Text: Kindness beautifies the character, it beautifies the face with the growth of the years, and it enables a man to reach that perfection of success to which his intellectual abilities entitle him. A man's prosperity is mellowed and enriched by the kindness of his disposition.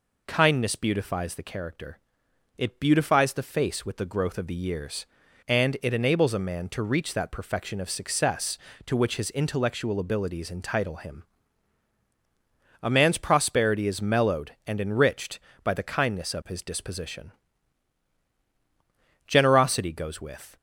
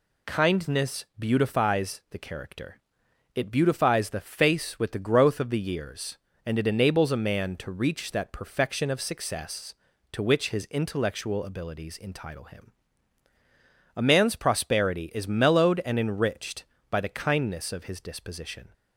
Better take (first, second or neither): second